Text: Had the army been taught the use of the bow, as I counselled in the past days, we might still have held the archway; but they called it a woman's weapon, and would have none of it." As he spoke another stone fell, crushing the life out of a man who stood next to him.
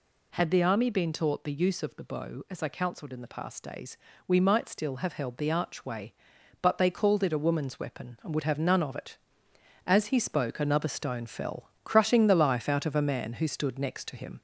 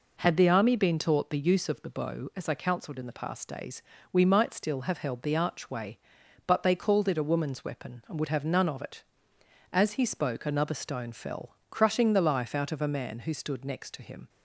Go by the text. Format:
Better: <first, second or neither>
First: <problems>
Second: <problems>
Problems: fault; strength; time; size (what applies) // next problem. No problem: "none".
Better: second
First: gets louder; slight; throughout; 2 dB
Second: none